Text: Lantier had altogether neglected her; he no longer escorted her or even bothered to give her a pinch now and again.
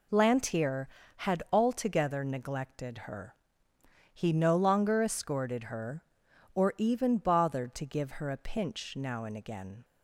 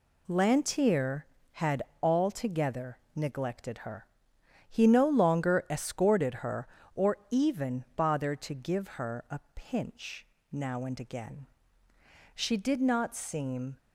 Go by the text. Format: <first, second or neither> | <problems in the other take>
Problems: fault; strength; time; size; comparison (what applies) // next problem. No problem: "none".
first | pauses between "had" and "altogether"; slight; at 1.8 s; 0.18 s long // pauses between "altogether" and "neglected"; slight; at 2.9 s; 0.18 s long // pauses between "pinch" and "now"; slight; at 10.2 s; 0.26 s long // goes on to say "She did not seem"; from 12.3 s on; 1.4 s long